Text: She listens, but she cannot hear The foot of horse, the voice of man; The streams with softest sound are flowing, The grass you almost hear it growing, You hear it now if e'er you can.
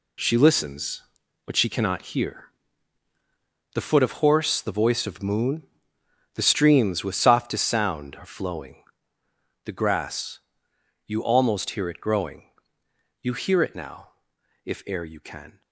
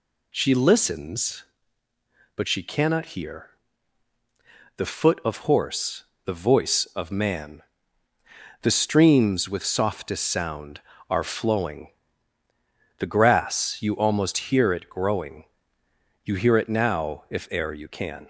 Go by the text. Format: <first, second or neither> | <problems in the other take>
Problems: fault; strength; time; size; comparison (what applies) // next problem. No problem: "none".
second | pauses between "hear" and "The"; at 2.5 s; 1.2 s long; strong in the second // says "moon" for "man"; at 5.2 s // pauses between "grass" and "you"; noticeable; at 10.3 s; 0.68 s long // pauses between "now" and "if"; noticeable; at 14.0 s; 0.56 s long